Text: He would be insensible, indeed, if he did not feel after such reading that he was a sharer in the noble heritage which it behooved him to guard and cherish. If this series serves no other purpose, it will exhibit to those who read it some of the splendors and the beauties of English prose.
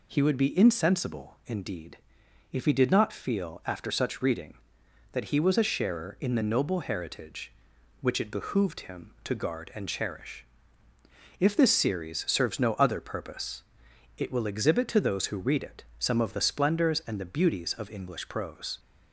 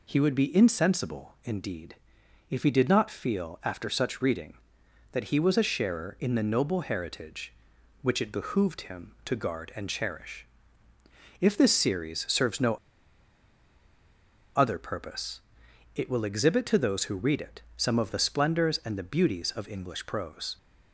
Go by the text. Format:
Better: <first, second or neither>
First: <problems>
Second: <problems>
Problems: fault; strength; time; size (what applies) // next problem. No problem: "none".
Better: first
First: pauses between "it" and "some"; slight; at 15.8 s; 0.16 s long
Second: pauses between "no" and "other"; strong; at 12.7 s; 1.8 s long // pauses between "it" and "some"; slight; at 17.6 s; 0.16 s long